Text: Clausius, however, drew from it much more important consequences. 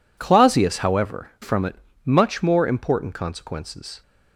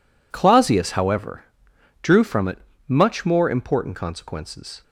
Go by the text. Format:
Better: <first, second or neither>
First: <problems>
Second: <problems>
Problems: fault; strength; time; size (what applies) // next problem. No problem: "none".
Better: second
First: skips "drew"; at 1.3 s // pauses between "it" and "much"; slight; at 1.7 s; 0.28 s long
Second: pauses between "it" and "much"; slight; at 2.5 s; 0.28 s long